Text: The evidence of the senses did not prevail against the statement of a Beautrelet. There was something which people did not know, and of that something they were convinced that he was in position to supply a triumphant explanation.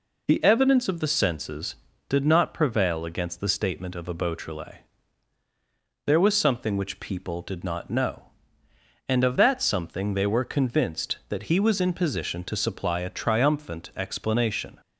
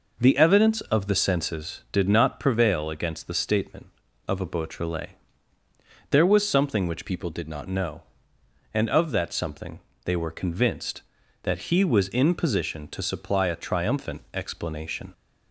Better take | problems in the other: first | changes voice from "people" to "not"; from 7.0 to 7.6 s; 0.6 s long // pauses between "something" and "they"; slight; at 9.8 s; 0.24 s long

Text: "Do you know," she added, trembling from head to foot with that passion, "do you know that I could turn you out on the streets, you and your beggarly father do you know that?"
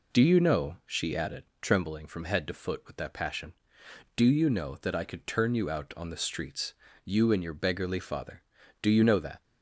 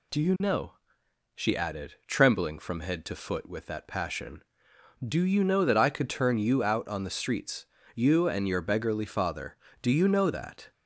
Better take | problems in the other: neither | none

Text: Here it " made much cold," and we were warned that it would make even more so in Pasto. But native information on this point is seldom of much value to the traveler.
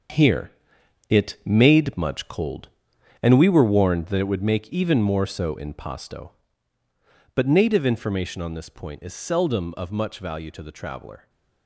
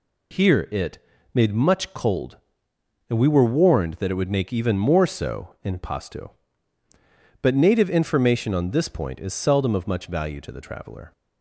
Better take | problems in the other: second | gets quieter; strong; throughout; 9.5 dB // pauses between "Here" and "it"; noticeable; at 0.5 s; 0.58 s long

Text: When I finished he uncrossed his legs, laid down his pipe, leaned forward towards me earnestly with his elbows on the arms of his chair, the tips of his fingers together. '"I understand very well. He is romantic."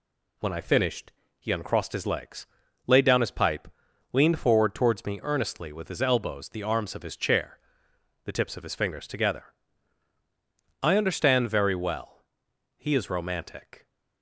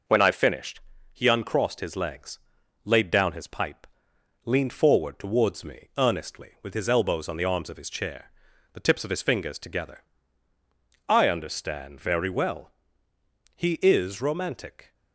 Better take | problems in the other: second | pauses between "finished" and "he"; slight; at 1.1 s; 0.28 s long; slight in the second // skips "on"; at 6.4 s

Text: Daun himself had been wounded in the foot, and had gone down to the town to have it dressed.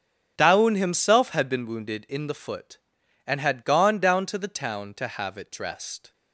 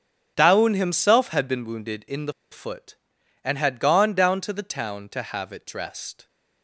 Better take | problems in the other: first | starts louder than the rest; strong; until 1.3 s; 8.5 dB; strong in the first // pauses between "the" and "foot"; slight; at 2.3 s; 0.18 s long

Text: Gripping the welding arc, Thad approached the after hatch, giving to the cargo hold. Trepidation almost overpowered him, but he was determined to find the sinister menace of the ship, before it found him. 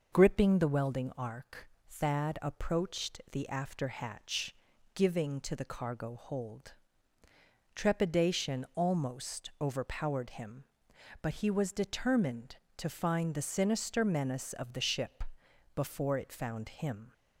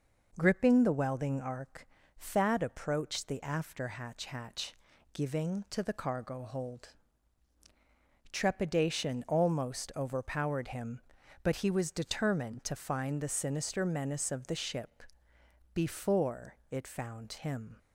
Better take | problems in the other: first | says "hatch" twice; at 4.2 s

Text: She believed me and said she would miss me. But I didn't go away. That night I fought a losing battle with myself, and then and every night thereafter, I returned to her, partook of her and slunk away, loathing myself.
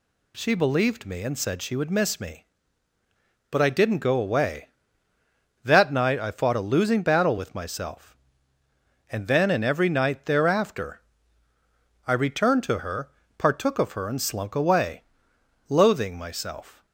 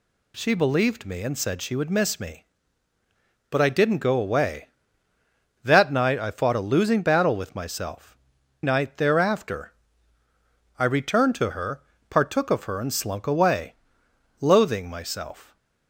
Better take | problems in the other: first | skips "and then and every"; at 8.4 s

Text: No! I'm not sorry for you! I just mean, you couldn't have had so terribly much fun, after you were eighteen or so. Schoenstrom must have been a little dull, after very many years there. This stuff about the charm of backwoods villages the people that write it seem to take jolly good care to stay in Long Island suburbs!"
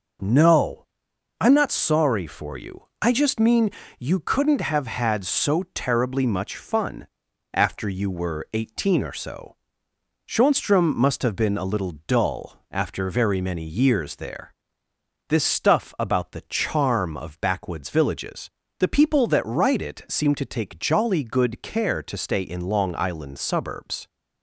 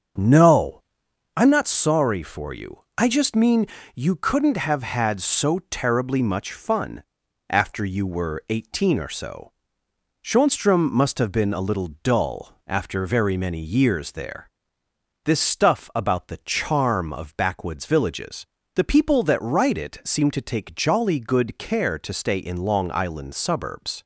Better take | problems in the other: first | starts louder than the rest; until 1.4 s; 7 dB // pauses between "villages" and "the"; slight; at 18.4 s; 0.28 s long; slight in the first

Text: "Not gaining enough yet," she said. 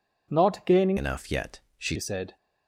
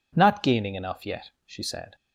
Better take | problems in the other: second | changes voice from "enough" to "she"; from 0.9 to 1.9 s; 1.0 s long

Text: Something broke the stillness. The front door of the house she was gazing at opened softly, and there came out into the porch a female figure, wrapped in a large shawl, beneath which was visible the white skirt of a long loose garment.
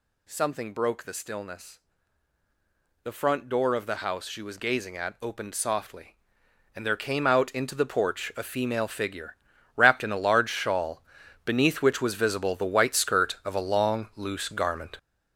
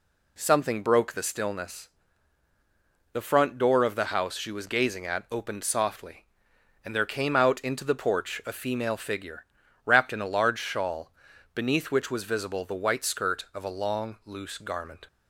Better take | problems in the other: second | gets louder; strong; throughout; 8.5 dB

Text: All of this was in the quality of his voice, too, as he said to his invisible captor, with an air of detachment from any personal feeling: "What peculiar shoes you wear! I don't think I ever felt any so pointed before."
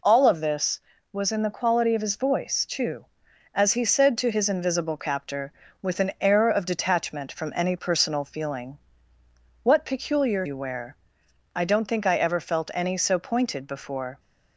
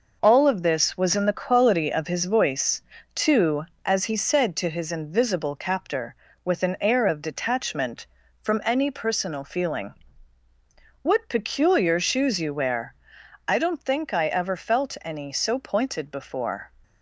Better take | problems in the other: second | skips "shoes"; at 10.4 s

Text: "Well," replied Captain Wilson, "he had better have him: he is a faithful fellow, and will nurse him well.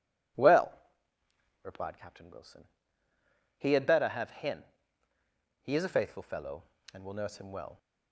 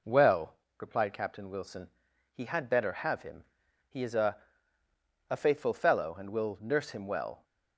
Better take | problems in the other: first | says "a" twice; at 5.2 s

